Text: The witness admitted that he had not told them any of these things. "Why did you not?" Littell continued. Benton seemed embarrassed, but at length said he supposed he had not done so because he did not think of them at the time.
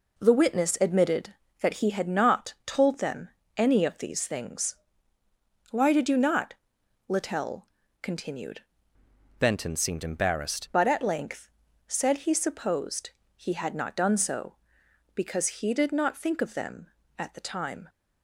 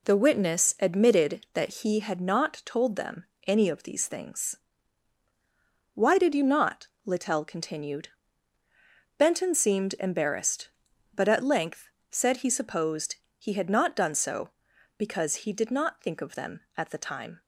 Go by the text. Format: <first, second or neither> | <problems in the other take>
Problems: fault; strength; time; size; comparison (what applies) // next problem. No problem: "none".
second | pauses between "them" and "any"; slight; at 3.2 s; 0.30 s long; slight in the second // pauses between "Littell" and "continued"; slight; at 7.6 s; 0.32 s long // changes voice from "Benton" to "embarrassed"; from 9.3 to 10.6 s; 1.3 s long // pauses between "length" and "said"; at 11.4 s; 0.38 s long; slight in the second // pauses between "supposed" and "he"; slight; at 13.1 s; 0.26 s long; slight in the second